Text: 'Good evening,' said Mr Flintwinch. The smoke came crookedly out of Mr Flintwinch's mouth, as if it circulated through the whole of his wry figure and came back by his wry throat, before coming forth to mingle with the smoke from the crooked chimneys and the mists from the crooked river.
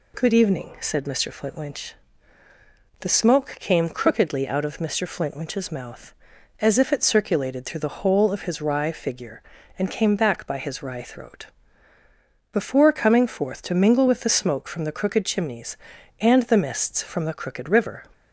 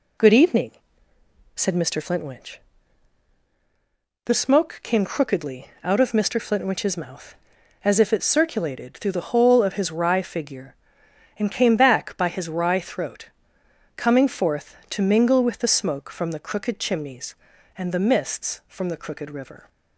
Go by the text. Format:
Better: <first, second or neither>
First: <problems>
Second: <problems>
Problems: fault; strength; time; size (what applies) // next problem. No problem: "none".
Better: first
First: none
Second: pauses between "crookedly" and "out"; slight; at 5.6 s; 0.18 s long // skips "before"; at 13.6 s